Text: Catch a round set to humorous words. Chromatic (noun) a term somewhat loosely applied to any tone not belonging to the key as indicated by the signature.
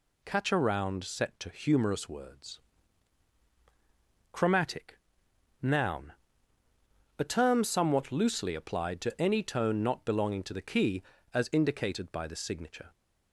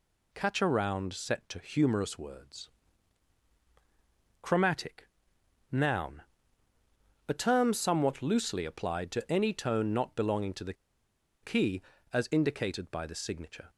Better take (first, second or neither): first